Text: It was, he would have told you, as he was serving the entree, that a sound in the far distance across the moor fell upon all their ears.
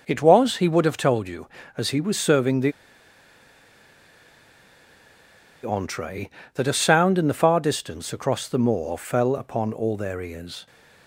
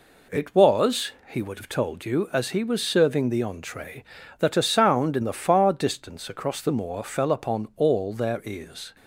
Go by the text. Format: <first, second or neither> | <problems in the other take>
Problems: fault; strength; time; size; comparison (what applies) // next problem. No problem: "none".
second | pauses between "the" and "entree"; strong; at 2.7 s; 2.9 s long